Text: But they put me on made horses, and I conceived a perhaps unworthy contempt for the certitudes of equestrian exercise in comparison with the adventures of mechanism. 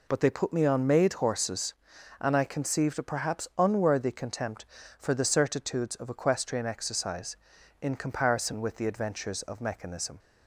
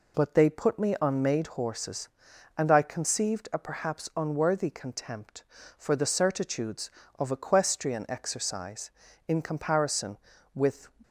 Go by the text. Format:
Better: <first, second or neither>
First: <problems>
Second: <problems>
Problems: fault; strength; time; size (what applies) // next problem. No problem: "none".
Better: first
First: none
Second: stops before "the adventures of mechanism"; at 11.0 s